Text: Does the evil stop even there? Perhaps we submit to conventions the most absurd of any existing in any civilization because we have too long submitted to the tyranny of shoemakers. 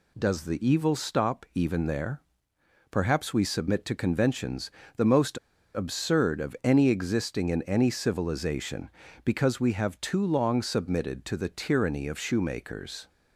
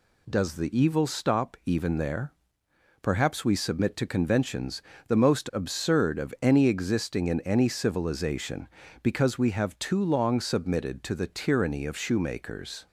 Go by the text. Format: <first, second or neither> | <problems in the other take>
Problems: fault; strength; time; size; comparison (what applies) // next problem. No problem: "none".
second | pauses between "conventions" and "the"; slight; at 4.6 s; 0.28 s long; slight in the second // pauses between "most" and "absurd"; slight; at 5.3 s; 0.35 s long